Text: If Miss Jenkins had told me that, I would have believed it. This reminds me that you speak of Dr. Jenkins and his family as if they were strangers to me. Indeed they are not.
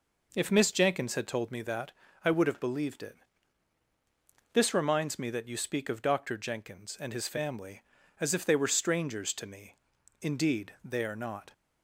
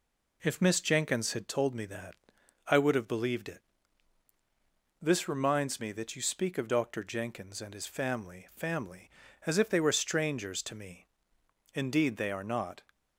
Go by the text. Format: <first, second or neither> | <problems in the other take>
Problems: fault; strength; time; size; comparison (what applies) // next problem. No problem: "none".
first | says "family" twice; at 8.5 s